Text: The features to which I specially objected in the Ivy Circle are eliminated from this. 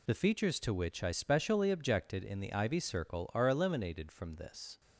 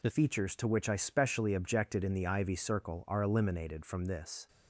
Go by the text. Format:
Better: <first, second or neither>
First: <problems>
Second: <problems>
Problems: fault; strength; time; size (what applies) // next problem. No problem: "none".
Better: first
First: none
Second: changes voice at "features"; from 0.1 s on; 4.3 s long